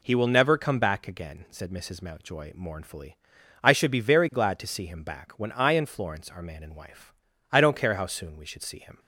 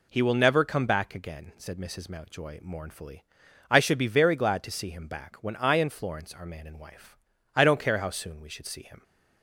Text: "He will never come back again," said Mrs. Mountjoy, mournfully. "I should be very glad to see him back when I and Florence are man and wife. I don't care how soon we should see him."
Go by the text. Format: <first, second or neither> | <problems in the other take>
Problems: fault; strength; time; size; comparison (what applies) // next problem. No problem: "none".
neither | none